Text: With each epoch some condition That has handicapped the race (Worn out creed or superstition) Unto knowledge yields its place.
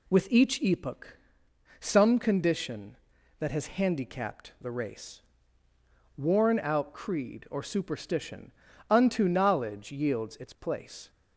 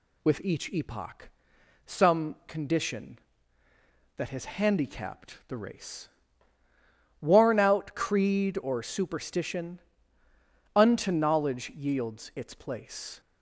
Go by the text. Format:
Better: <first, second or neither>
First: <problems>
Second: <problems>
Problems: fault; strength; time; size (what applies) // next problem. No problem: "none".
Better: neither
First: pauses between "epoch" and "some"; noticeable; at 1.1 s; 0.62 s long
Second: pauses between "epoch" and "some"; noticeable; at 1.3 s; 0.56 s long